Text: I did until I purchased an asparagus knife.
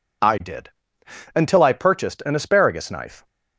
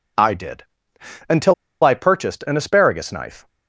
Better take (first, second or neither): first